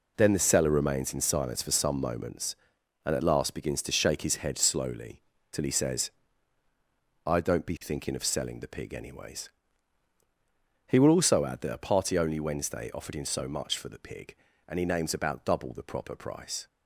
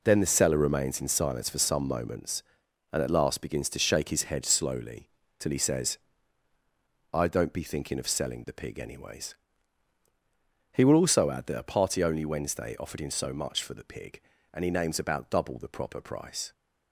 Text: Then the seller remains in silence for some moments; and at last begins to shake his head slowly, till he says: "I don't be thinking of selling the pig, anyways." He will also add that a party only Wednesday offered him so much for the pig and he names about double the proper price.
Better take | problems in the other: neither | none

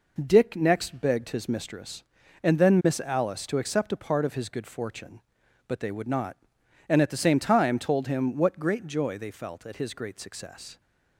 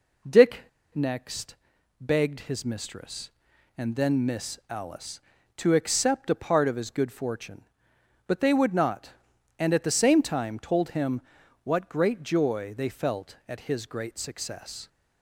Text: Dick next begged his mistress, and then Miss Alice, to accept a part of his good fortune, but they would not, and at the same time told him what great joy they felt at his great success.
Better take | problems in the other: first | pauses between "Dick" and "next"; slight; at 0.6 s; 0.32 s long // pauses between "next" and "begged"; noticeable; at 1.5 s; 0.46 s long // pauses between "him" and "what"; at 11.1 s; 0.44 s long

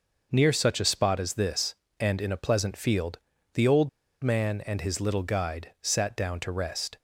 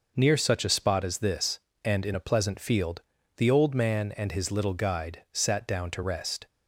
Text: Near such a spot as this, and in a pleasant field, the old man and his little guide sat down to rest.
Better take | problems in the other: second | pauses between "old" and "man"; slight; at 3.8 s; 0.35 s long

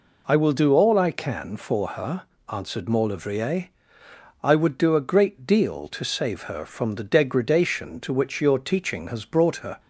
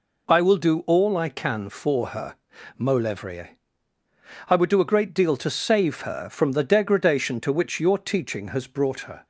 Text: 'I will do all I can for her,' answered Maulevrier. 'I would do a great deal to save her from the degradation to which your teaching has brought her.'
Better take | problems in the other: first | skips "answered"; at 2.5 s

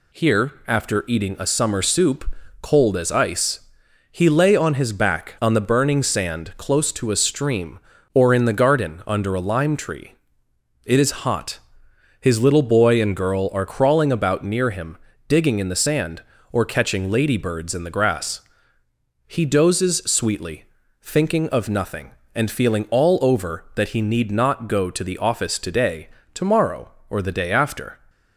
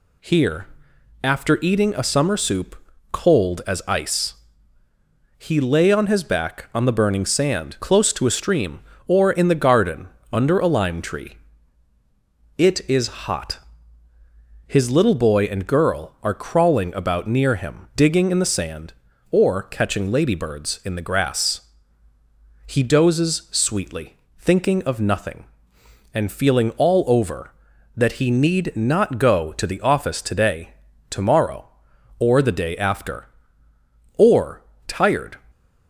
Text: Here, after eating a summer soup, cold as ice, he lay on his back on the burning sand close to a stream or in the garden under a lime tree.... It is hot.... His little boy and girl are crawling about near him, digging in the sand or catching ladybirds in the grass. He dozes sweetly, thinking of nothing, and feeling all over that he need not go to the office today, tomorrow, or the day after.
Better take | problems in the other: first | pauses between "garden" and "under"; slight; at 10.0 s; 0.24 s long // goes on to say "Or tired"; noticeable; from 34.1 s on; 1.2 s long // stays silent after the last word; slight; from 35.3 s on; 0.5 s long

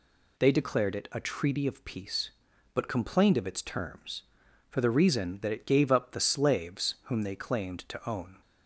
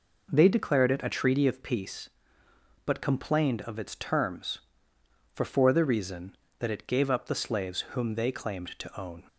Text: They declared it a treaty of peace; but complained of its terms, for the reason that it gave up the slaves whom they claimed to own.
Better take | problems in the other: first | says "for" twice; at 5.4 s

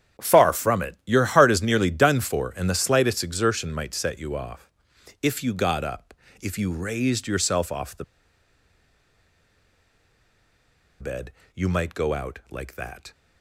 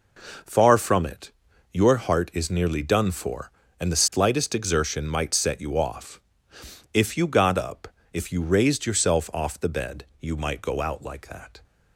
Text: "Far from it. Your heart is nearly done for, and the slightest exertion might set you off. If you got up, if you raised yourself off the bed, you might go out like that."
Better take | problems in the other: second | starts louder than the rest; strong; until 1.3 s; 9 dB // pauses between "the" and "bed"; strong; at 8.0 s; 2.9 s long

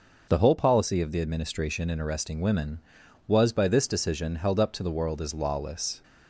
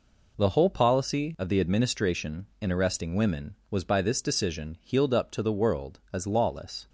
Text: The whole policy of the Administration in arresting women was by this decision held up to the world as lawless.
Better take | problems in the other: first | says "healed" for "held"; at 4.8 s

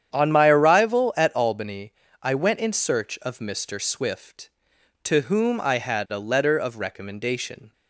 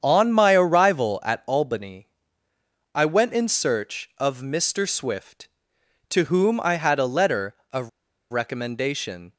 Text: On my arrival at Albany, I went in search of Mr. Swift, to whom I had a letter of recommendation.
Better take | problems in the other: first | starts louder than the rest; strong; until 1.0 s; 8 dB; strong in the first // pauses between "of" and "recommendation"; at 7.8 s; 0.41 s long

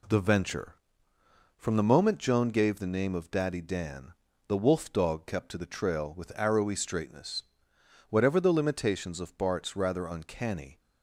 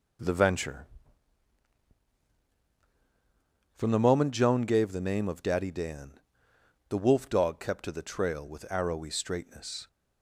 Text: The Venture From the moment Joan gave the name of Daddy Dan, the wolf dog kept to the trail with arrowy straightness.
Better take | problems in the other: second | goes on to say "Whatever the limitations of Bart's rather uncanny"; strong; from 8.0 s on; 2.7 s long

